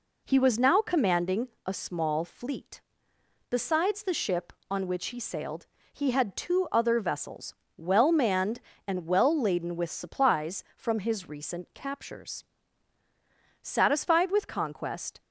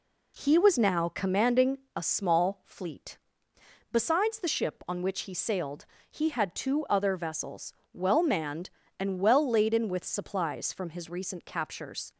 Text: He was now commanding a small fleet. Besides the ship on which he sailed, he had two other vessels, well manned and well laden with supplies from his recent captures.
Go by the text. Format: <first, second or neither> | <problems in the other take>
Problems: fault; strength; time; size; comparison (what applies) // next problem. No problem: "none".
second | pauses between "commanding" and "a"; slight; at 1.4 s; 0.18 s long; slight in the second // goes on to say "Satisfied with conquest"; from 13.6 s on; 1.5 s long